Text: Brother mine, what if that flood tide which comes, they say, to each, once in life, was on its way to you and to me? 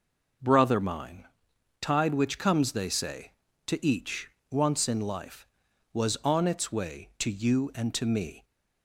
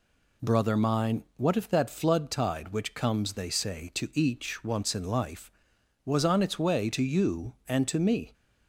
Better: second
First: skips "what if that flood"; at 1.5 s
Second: none

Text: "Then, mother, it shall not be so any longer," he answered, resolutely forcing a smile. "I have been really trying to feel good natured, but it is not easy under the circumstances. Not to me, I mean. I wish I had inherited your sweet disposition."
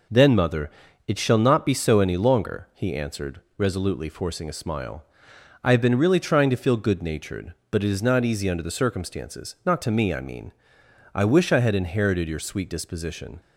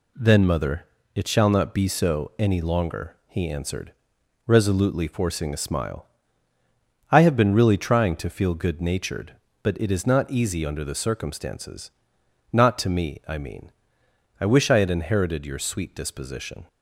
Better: neither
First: none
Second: none

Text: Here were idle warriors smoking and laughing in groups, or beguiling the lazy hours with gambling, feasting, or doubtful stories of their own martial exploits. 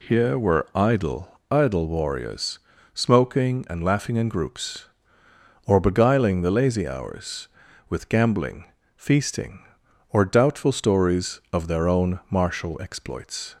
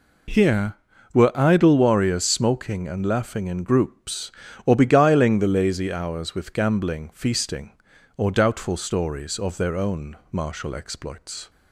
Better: second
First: says "idle" twice; at 1.5 s // pauses between "warriors" and "smoking"; slight; at 2.5 s; 0.34 s long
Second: none

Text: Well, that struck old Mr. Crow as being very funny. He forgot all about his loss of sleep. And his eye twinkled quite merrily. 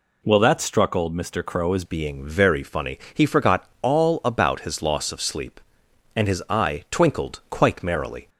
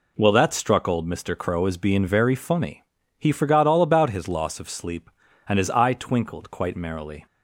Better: second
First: changes voice at "being"; from 1.8 s on; 6.4 s long // pauses between "forgot" and "all"; slight; at 3.6 s; 0.18 s long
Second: none

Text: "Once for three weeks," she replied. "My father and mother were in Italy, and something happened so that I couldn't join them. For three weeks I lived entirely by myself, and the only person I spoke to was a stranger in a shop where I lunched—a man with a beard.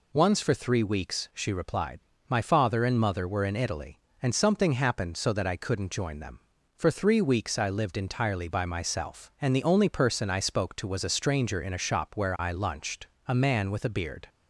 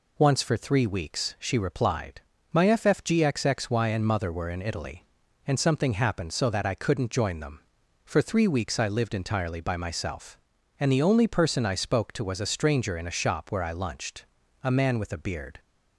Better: first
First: none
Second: says "ffgxxy" for "father"; at 2.6 s

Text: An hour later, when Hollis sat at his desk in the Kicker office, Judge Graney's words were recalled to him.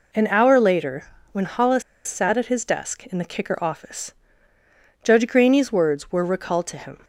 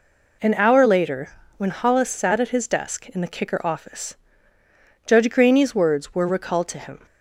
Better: second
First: pauses between "Hollis" and "sat"; slight; at 1.8 s; 0.25 s long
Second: none

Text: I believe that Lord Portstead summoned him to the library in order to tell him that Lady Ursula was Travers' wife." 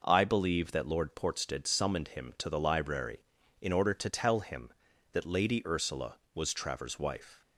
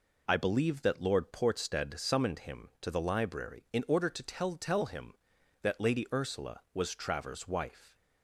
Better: first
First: none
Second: says "tell" twice; at 4.5 s

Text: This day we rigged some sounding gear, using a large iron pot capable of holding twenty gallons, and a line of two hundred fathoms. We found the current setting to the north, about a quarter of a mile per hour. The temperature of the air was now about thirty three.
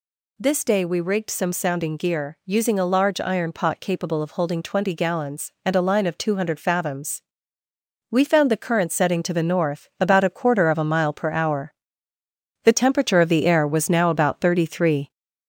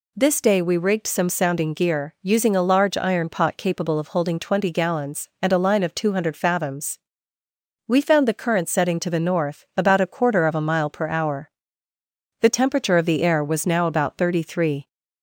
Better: second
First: gets louder; slight; throughout; 3 dB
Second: none

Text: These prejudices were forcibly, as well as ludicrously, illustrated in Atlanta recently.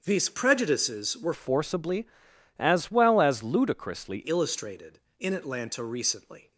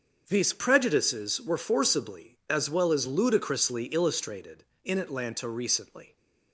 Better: second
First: starts louder than the rest; until 1.0 s; 7 dB // changes voice from "forcibly" to "ludicrously"; from 1.3 to 4.2 s; 2.9 s long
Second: starts louder than the rest; until 1.2 s; 7 dB

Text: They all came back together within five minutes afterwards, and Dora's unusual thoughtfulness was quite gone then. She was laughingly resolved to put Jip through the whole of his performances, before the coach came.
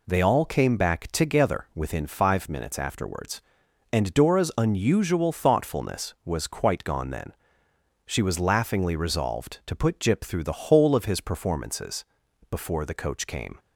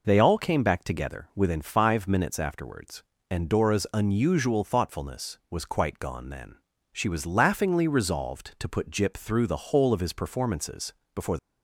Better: first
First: none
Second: stops before "the coach came"; at 11.3 s

